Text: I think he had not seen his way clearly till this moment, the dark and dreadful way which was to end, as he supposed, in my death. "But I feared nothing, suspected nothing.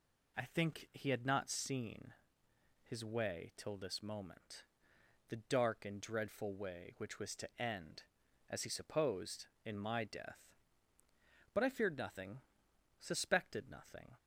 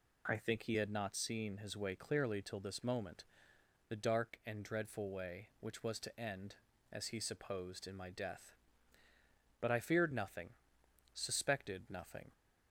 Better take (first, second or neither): second